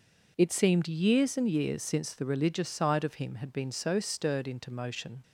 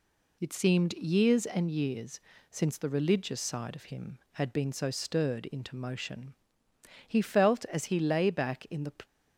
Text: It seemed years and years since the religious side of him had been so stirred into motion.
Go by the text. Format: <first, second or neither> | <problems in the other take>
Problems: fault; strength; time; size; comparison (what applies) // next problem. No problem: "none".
first | pauses between "years" and "since"; slight; at 2.2 s; 0.30 s long // goes on to say "He felt as he lay back in the"; strong; from 7.0 s on; 1.8 s long